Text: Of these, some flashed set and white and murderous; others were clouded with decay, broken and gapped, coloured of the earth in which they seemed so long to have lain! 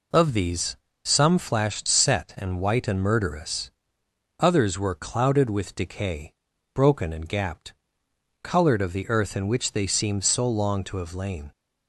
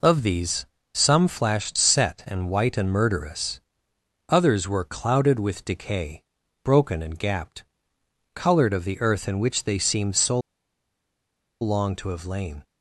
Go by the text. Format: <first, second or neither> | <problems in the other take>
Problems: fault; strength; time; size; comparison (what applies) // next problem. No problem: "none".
first | pauses between "so" and "long"; at 10.4 s; 1.2 s long